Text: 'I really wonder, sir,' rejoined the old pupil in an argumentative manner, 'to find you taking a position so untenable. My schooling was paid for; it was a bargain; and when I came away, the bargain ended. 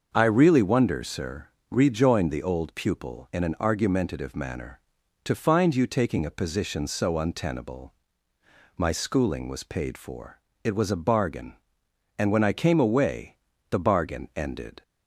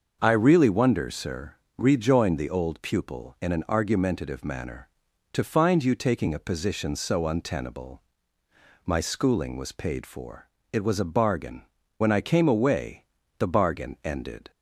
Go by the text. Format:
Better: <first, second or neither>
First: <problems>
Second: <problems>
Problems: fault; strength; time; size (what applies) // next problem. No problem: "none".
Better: first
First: starts louder than the rest; until 1.1 s; 6.5 dB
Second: starts louder than the rest; until 1.2 s; 6.5 dB // skips "and"; at 11.8 s